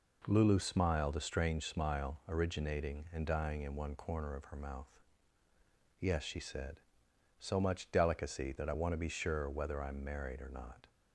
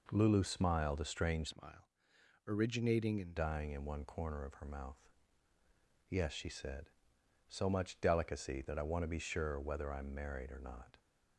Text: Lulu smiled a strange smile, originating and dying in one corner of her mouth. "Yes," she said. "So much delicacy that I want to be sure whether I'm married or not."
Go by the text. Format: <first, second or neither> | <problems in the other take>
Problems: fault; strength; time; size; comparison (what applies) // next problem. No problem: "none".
first | changes voice from "smile" to "and"; from 1.4 to 3.3 s; 1.9 s long